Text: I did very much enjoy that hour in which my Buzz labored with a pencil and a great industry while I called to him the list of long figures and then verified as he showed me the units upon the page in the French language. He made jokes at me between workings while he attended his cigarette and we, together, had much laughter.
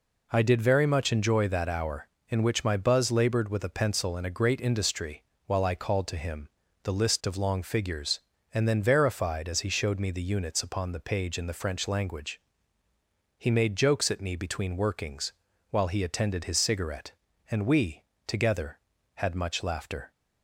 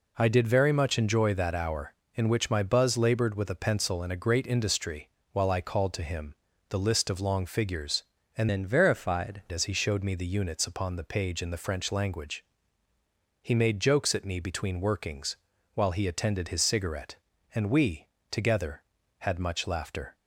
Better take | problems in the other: first | pauses between "industry" and "while"; slight; at 5.0 s; 0.24 s long; slight in the first // pauses between "him" and "the"; slight; at 6.3 s; 0.34 s long; slight in the first // changes voice from "then" to "verified"; from 8.4 to 9.4 s; 1.0 s long // pauses between "workings" and "while"; at 15.3 s; 0.38 s long; also in the first

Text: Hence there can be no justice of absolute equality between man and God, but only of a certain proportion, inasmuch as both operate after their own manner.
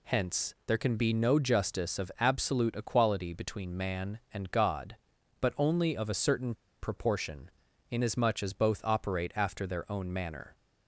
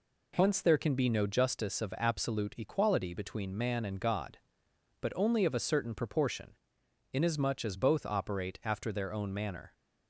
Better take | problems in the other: second | pauses between "certain" and "proportion"; slight; at 6.5 s; 0.28 s long

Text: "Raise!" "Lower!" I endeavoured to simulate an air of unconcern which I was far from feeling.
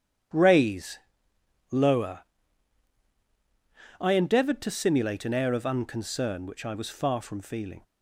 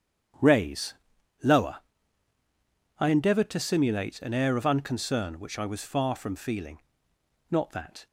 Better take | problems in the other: first | starts louder than the rest; strong; until 3.1 s; 9 dB; strong in the first // goes on to say "Not that"; from 7.5 s on; 0.56 s long

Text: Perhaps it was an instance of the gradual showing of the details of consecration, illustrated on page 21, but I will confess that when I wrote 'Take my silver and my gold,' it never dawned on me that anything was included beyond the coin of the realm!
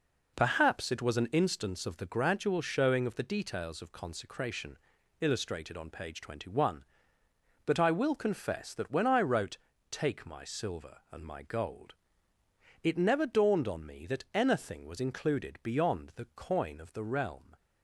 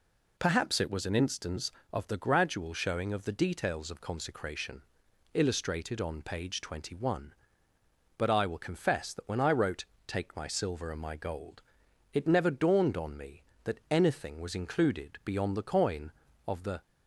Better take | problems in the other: first | pauses between "wrote" and "Take"; slight; at 9.8 s; 0.22 s long; slight in the first // stops before "realm"; at 16.8 s

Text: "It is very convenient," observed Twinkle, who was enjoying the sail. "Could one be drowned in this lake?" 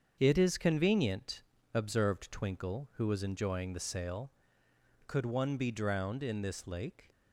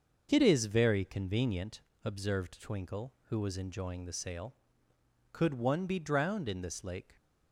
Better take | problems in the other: second | starts louder than the rest; until 1.2 s; 7 dB; noticeable in the second // skips "very"; at 0.5 s

